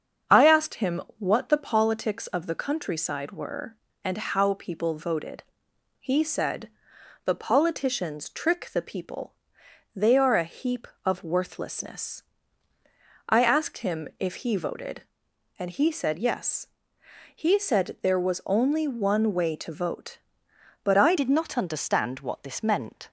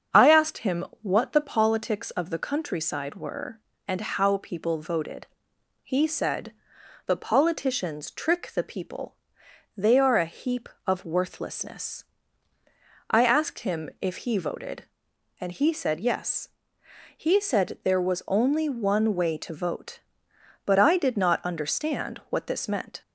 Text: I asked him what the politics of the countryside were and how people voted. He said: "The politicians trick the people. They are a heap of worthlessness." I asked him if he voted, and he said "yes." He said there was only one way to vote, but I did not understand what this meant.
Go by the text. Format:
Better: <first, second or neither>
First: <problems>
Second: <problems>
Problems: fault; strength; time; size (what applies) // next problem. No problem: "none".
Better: second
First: starts louder than the rest; until 1.5 s; 7 dB // pauses between "him" and "what"; slight; at 0.9 s; 0.20 s long // changes voice at "did"; from 21.1 s on; 1.9 s long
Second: starts louder than the rest; until 1.3 s; 7 dB // pauses between "him" and "what"; slight; at 0.8 s; 0.20 s long